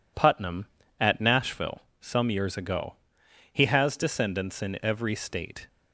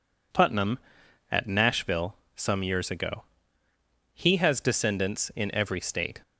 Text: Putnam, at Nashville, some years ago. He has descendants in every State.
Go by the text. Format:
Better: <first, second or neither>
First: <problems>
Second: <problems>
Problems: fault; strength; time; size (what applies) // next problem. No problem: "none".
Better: neither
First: none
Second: none